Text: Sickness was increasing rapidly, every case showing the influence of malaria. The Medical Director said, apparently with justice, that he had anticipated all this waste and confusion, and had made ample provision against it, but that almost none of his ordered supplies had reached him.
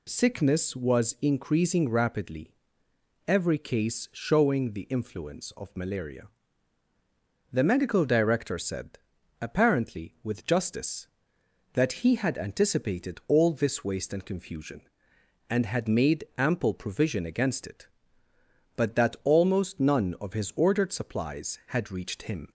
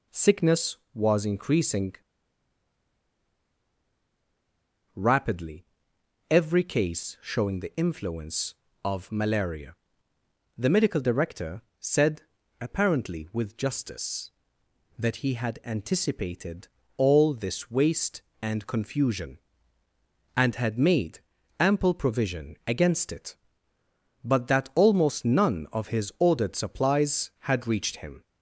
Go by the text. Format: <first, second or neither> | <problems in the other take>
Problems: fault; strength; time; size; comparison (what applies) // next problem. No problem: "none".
first | pauses between "increasing" and "rapidly"; strong; at 1.9 s; 3.0 s long // pauses between "Director" and "said"; slight; at 11.6 s; 0.18 s long // pauses between "anticipated" and "all"; slight; at 16.6 s; 0.30 s long // pauses between "made" and "ample"; at 21.1 s; 0.40 s long